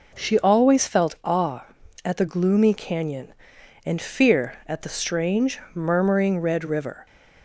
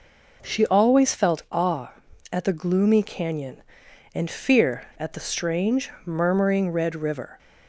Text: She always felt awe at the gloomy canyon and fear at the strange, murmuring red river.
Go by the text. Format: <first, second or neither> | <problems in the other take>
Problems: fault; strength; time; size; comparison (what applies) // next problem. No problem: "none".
neither | none